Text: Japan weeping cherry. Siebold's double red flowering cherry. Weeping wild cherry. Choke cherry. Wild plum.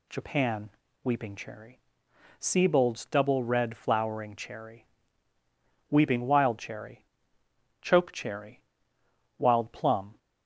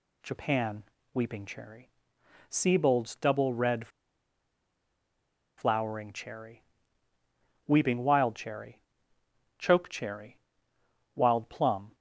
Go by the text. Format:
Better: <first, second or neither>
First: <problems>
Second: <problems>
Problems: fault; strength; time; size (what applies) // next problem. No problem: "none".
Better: first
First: pauses between "Japan" and "weeping"; slight; at 0.7 s; 0.33 s long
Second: pauses between "Japan" and "weeping"; slight; at 0.8 s; 0.30 s long // pauses between "red" and "flowering"; strong; at 3.8 s; 1.6 s long